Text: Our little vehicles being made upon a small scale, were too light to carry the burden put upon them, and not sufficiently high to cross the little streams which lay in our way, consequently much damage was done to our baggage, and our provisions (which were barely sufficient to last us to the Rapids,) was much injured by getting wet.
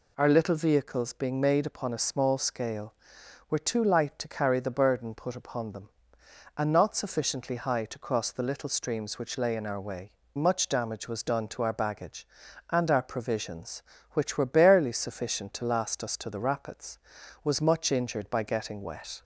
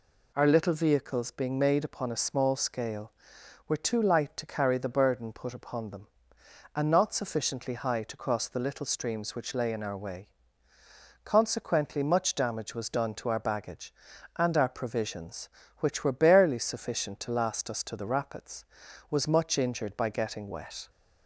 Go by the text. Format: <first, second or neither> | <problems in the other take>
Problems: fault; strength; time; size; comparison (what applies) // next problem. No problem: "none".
second | skips "consequently"; at 10.2 s